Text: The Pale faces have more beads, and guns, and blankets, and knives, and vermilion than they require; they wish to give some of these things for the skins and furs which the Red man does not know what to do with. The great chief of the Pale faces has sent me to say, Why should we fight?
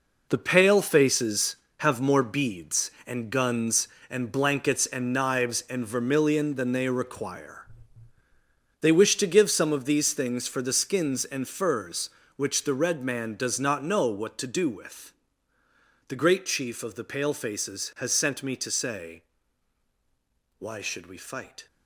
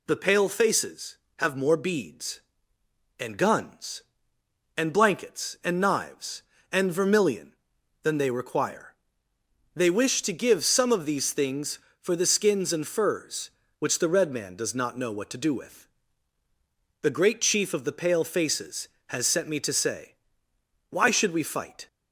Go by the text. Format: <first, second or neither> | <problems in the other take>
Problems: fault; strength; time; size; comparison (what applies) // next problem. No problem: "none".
second | gets quieter; strong; throughout; 9.5 dB